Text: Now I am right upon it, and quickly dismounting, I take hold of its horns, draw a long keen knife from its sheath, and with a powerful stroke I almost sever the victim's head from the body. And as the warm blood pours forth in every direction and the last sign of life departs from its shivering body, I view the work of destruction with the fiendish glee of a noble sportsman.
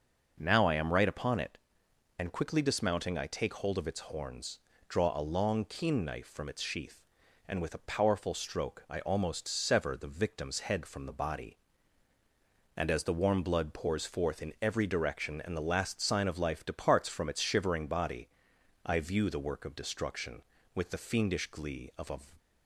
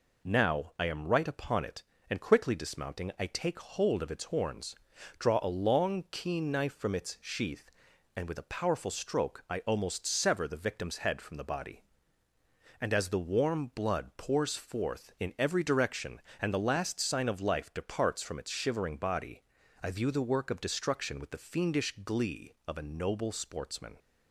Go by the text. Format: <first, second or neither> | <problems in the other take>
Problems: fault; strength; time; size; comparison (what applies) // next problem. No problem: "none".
second | stops before "noble sportsman"; at 22.3 s